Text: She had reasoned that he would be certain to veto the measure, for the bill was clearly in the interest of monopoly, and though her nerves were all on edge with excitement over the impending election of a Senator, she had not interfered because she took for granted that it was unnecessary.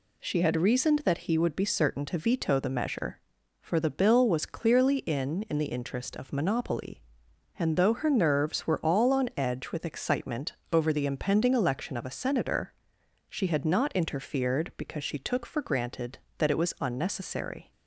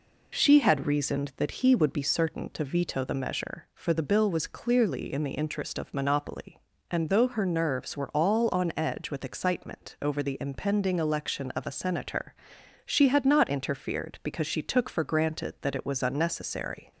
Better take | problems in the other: second | says "in" twice; at 5.4 s // pauses between "excitement" and "over"; slight; at 10.5 s; 0.18 s long

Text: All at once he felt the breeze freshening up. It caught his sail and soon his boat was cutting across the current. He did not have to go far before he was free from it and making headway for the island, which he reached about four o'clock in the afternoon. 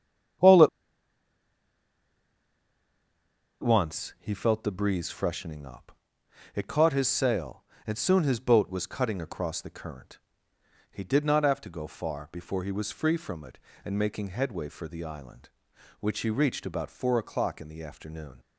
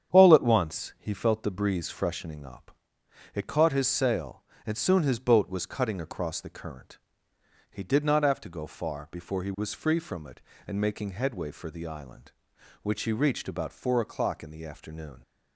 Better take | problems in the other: second | starts louder than the rest; strong; until 4.4 s; 8.5 dB; strong in the second // pauses between "at" and "once"; strong; at 0.6 s; 2.9 s long

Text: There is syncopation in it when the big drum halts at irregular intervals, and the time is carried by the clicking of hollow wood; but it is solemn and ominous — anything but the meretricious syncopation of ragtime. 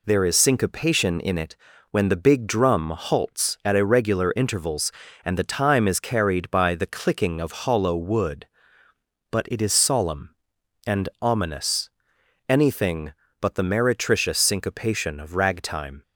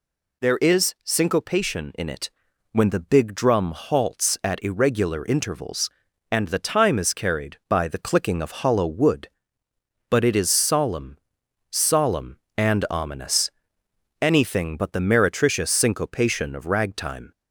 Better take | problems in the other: first | pauses between "it" and "when"; at 2.2 s; 0.44 s long; slight in the first // says "solemn" twice; at 11.7 s

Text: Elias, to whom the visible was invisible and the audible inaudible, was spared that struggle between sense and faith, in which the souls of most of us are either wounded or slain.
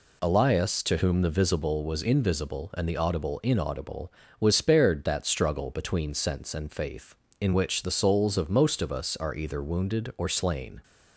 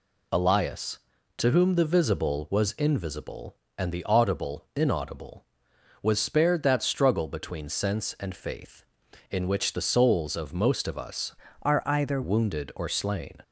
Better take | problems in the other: first | changes voice from "are" to "either"; from 11.6 to 12.2 s; 0.6 s long

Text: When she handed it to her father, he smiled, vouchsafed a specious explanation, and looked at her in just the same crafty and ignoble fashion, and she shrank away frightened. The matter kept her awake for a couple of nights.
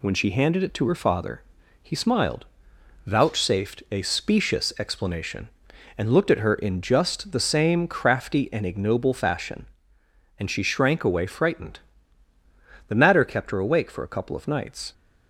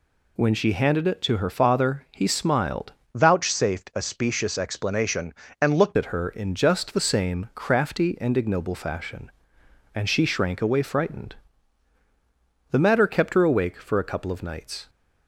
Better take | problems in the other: first | changes voice from "vouchsafed" to "looked"; from 3.1 to 5.9 s; 2.8 s long

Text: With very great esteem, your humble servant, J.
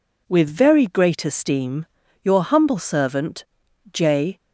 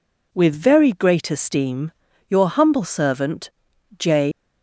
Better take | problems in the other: first | leaves "J" unfinished; at 4.3 s; 135 ms

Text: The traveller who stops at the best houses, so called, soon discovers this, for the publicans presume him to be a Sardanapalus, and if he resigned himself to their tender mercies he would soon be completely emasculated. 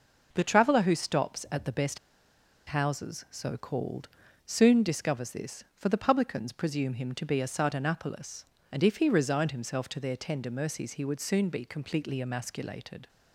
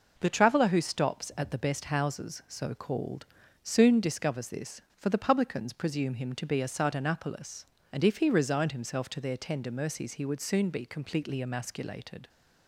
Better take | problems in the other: second | pauses between "best" and "houses"; noticeable; at 1.9 s; 0.69 s long

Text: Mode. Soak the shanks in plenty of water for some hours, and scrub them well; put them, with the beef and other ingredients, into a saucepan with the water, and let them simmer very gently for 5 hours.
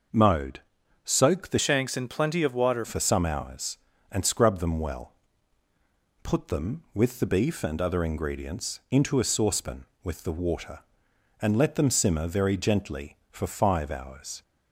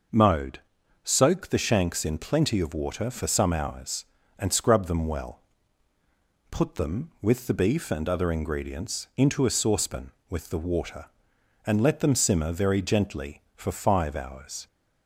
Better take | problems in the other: second | changes voice from "shanks" to "water"; from 1.5 to 2.8 s; 1.3 s long

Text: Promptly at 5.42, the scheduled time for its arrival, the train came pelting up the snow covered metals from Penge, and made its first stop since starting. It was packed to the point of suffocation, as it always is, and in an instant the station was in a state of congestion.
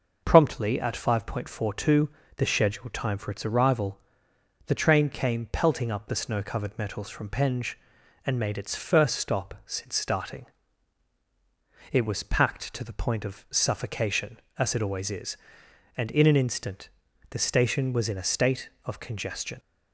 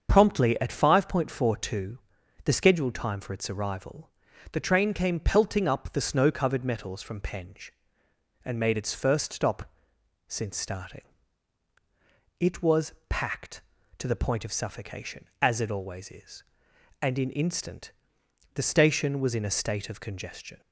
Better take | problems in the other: first | starts louder than the rest; until 1.1 s; 7 dB // pauses between "stop" and "since"; noticeable; at 9.7 s; 0.54 s long // pauses between "was" and "packed"; slight; at 12.9 s; 0.16 s long // skips "an"; at 17.3 s // pauses between "instant" and "the"; noticeable; at 17.9 s; 0.62 s long; also in the first

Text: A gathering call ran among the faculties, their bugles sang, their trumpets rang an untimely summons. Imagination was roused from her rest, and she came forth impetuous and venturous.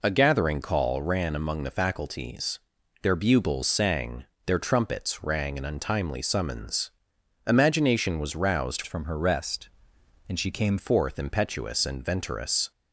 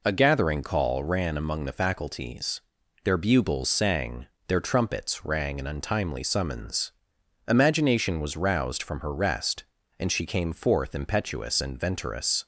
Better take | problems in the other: second | changes voice from "from" to "came"; from 8.8 to 10.7 s; 1.9 s long

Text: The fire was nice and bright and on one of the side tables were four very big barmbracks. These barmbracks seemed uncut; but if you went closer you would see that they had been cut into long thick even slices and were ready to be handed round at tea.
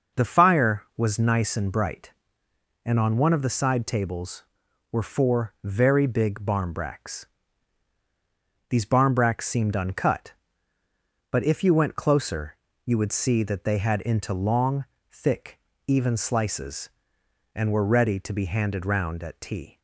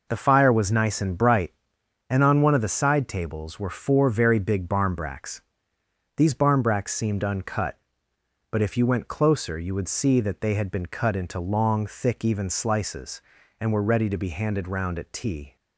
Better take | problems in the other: second | pauses between "closer" and "you"; slight; at 12.5 s; 0.28 s long // skips "been cut"; at 14.0 s // pauses between "long" and "thick"; slight; at 14.8 s; 0.26 s long // pauses between "thick" and "even"; slight; at 15.5 s; 0.28 s long

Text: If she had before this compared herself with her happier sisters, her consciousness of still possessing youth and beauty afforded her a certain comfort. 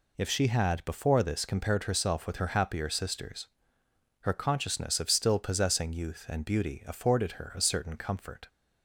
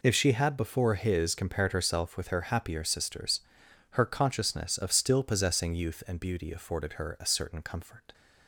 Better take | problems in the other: first | says "his" for "this"; at 0.9 s

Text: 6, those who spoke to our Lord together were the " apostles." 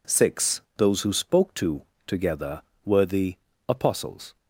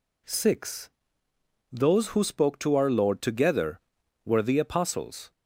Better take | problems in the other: second | skips "our Lord"; at 1.9 s

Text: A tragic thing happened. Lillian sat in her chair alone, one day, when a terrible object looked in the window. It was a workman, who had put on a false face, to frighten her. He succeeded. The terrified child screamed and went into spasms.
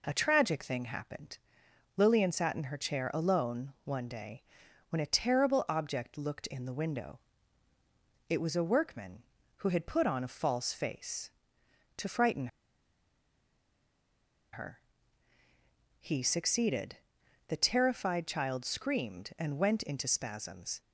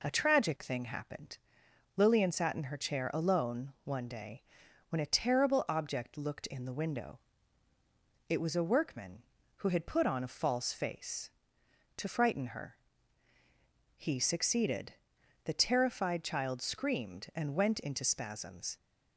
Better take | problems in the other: second | pauses between "frighten" and "her"; strong; at 12.4 s; 2.0 s long

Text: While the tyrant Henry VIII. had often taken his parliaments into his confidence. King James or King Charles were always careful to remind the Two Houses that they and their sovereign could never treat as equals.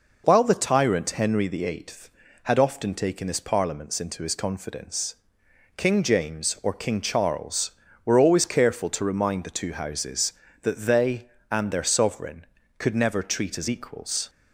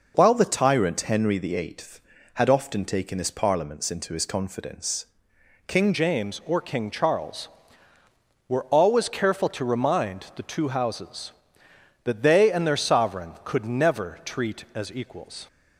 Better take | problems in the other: first | changes voice at "James"; from 5.9 s on; 9.5 s long

